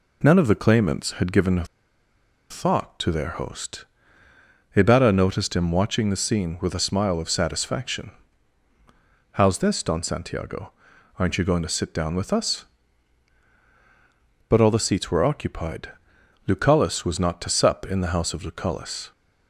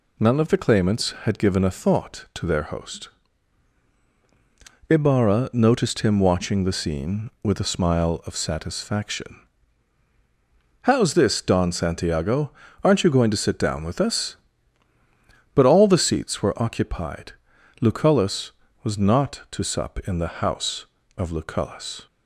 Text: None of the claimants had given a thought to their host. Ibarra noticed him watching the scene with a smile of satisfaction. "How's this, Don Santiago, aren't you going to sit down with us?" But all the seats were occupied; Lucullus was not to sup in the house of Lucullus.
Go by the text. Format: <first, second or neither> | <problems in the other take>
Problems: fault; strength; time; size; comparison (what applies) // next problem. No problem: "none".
second | pauses between "a" and "thought"; noticeable; at 1.6 s; 0.86 s long